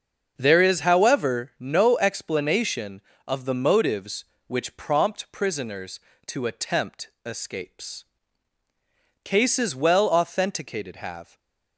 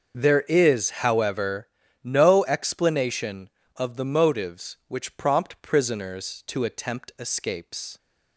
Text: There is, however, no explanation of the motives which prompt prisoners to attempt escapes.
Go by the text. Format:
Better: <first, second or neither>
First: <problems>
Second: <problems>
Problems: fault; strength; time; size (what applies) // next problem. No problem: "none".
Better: second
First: starts louder than the rest; until 1.3 s; 6.5 dB // pauses between "attempt" and "escapes"; slight; at 7.0 s; 0.16 s long // goes on to say "Cases well authenticated have"; strong; from 9.2 s on; 2.1 s long // stays silent after the last word; slight; from 11.2 s on; 0.5 s long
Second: starts louder than the rest; until 1.1 s; 6.5 dB